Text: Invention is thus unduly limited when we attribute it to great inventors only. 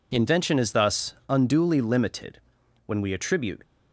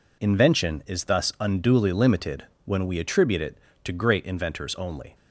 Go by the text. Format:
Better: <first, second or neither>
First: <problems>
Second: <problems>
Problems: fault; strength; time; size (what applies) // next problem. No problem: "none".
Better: second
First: pauses between "thus" and "unduly"; slight; at 1.1 s; 0.16 s long // pauses between "limited" and "when"; noticeable; at 2.3 s; 0.48 s long // stops before "it to great inventors only"; at 3.6 s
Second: pauses between "limited" and "when"; slight; at 2.4 s; 0.20 s long